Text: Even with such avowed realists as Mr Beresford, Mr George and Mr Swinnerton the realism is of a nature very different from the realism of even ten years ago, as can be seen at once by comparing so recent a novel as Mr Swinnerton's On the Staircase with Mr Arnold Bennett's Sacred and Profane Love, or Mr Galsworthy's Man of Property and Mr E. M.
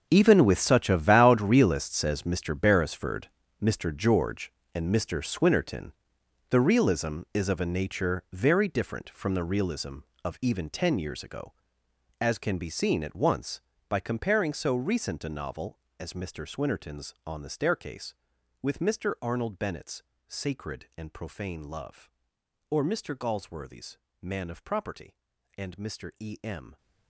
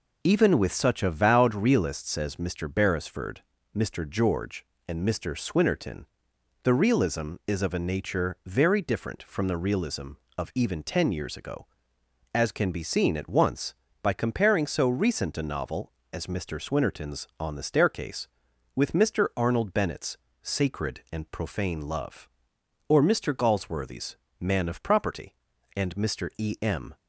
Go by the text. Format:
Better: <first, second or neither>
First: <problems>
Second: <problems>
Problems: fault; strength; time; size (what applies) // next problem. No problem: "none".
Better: second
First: gets quieter; strong; throughout; 15 dB // pauses between "Swinnerton" and "the"; noticeable; at 5.9 s; 0.58 s long // pauses between "Bennett's" and "Sacred"; slight; at 20.0 s; 0.24 s long // pauses between "Galsworthy's" and "Man"; slight; at 23.9 s; 0.24 s long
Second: pauses between "Swinnerton" and "the"; noticeable; at 6.0 s; 0.58 s long // pauses between "Bennett's" and "Sacred"; slight; at 20.1 s; 0.24 s long // pauses between "Galsworthy's" and "Man"; slight; at 24.1 s; 0.24 s long